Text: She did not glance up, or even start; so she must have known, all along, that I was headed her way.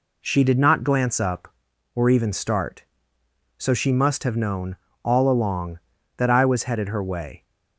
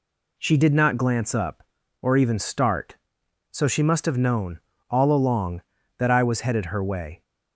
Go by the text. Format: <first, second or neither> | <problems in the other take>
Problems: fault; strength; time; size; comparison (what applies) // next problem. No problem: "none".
neither | none